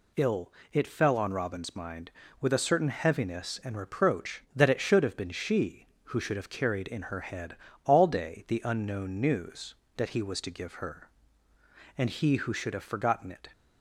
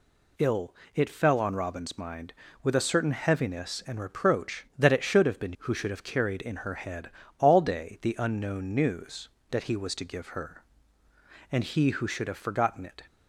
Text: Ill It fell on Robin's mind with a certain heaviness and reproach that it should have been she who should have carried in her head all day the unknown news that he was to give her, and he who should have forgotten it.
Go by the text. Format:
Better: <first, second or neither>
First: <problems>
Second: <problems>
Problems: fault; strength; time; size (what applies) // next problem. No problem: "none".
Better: first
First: pauses between "Ill" and "It"; slight; at 0.5 s; 0.18 s long // pauses between "head" and "all"; slight; at 7.5 s; 0.28 s long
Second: pauses between "Ill" and "It"; slight; at 0.7 s; 0.18 s long // skips "she"; at 5.5 s // pauses between "head" and "all"; slight; at 7.1 s; 0.28 s long